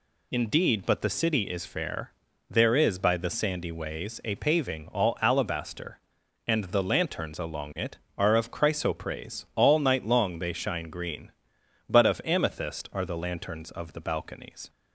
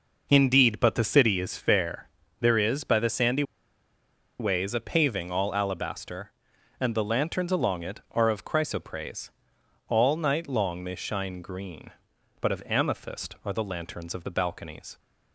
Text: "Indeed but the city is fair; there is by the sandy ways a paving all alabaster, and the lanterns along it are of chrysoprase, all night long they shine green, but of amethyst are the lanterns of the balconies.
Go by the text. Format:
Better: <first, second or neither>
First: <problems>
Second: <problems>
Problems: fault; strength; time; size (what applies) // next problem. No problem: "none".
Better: first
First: none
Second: pauses between "sandy" and "ways"; noticeable; at 3.4 s; 0.97 s long